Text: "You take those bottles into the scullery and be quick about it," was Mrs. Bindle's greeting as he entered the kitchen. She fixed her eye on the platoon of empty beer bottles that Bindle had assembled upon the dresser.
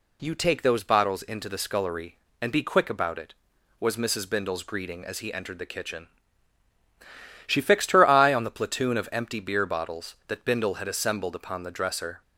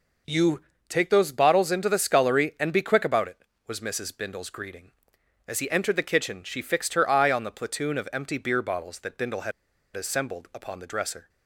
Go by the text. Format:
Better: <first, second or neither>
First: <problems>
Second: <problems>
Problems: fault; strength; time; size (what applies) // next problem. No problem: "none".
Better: first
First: none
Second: pauses between "You" and "take"; slight; at 0.6 s; 0.26 s long // pauses between "had" and "assembled"; at 9.5 s; 0.44 s long